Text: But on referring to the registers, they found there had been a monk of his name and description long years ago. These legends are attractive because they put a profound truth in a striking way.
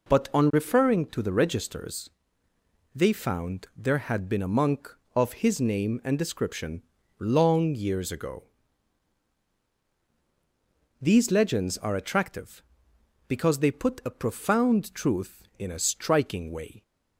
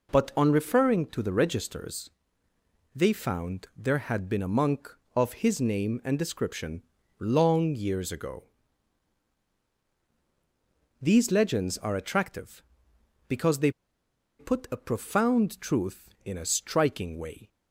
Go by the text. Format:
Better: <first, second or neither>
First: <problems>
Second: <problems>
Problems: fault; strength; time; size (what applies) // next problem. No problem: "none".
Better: first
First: pauses between "description" and "long"; at 6.8 s; 0.38 s long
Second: pauses between "description" and "long"; at 6.8 s; 0.38 s long // pauses between "they" and "put"; noticeable; at 13.6 s; 0.69 s long